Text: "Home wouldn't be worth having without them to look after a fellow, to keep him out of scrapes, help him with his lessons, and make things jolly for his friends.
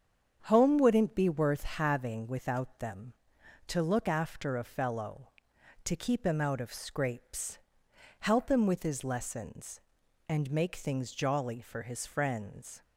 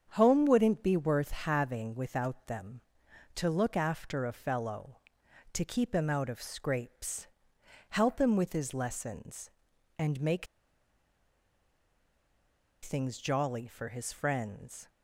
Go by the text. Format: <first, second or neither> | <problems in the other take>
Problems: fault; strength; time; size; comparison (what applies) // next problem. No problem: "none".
first | starts louder than the rest; strong; until 1.1 s; 7.5 dB; strong in the first // pauses between "make" and "things"; strong; at 10.4 s; 2.3 s long